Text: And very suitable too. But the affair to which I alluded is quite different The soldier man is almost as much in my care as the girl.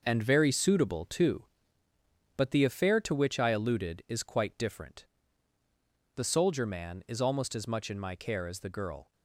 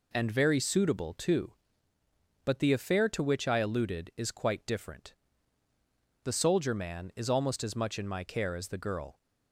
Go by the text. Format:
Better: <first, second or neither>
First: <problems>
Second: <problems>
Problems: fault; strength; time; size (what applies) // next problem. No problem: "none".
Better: second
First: gets quieter; strong; throughout; 8.5 dB // pauses between "different" and "The"; at 5.0 s; 1.1 s long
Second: pauses between "different" and "The"; at 5.1 s; 1.1 s long